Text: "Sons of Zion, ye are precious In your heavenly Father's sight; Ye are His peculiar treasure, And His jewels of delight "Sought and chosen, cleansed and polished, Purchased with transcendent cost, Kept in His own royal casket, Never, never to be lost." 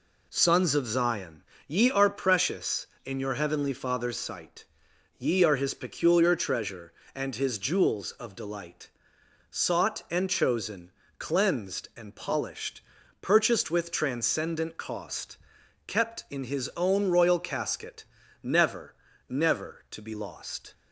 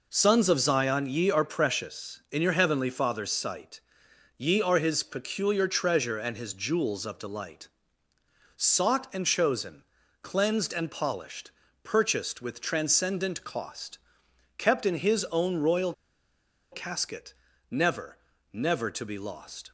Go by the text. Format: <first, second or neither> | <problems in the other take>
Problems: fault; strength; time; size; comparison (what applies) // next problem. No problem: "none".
first | pauses between "delight" and "Sought"; noticeable; at 7.6 s; 0.90 s long; noticeable in the first // pauses between "royal" and "casket"; noticeable; at 15.9 s; 0.78 s long